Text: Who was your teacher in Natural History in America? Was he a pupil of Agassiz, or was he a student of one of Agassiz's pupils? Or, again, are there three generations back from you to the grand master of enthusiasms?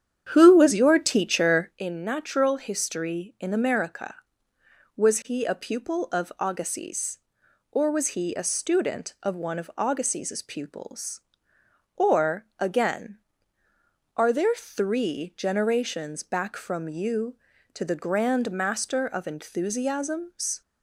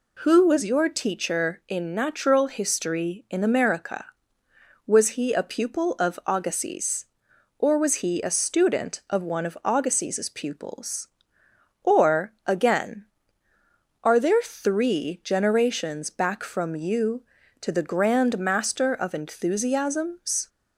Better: second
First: starts louder than the rest; strong; until 1.8 s; 9 dB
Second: none

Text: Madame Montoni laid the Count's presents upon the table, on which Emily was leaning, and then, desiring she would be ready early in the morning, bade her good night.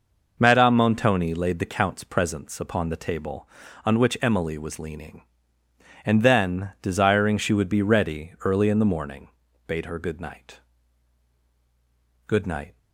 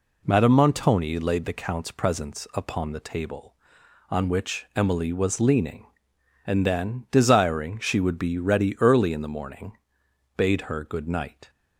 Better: second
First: goes on to say "Good night"; from 12.2 s on; 0.50 s long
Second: none

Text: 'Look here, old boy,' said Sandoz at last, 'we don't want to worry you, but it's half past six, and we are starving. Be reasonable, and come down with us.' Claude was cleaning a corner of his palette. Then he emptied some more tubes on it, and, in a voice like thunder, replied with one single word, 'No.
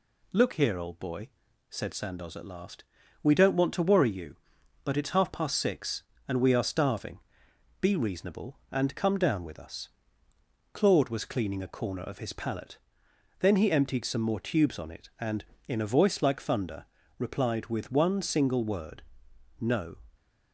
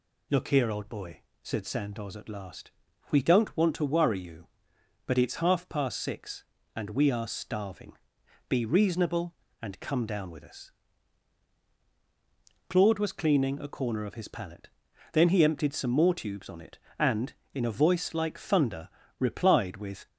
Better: first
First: none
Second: stops before "one single word No"; at 20.0 s

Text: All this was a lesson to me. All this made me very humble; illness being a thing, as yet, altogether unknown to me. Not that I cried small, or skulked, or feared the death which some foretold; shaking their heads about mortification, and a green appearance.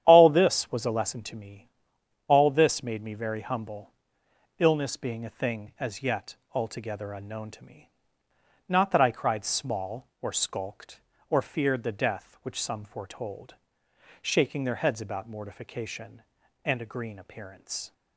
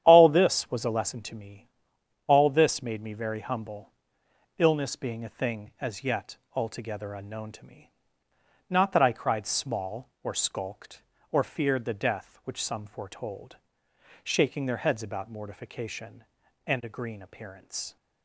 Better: neither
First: starts louder than the rest; strong; until 1.0 s; 10 dB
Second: starts louder than the rest; strong; until 1.0 s; 10 dB

